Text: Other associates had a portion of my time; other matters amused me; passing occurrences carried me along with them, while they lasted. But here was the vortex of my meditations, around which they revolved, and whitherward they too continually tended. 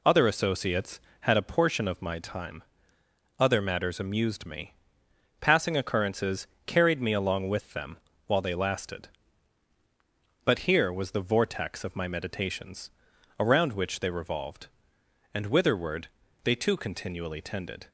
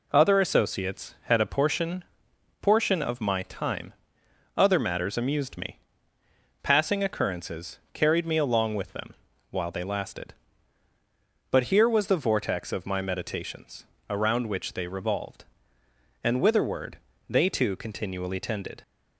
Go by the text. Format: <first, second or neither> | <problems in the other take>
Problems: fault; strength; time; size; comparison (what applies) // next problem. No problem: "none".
first | says "portion" twice; at 2.6 s // pauses between "occurrences" and "carried"; slight; at 7.7 s; 0.16 s long; slight in the first // pauses between "whitherward" and "they"; slight; at 16.9 s; 0.34 s long; also in the first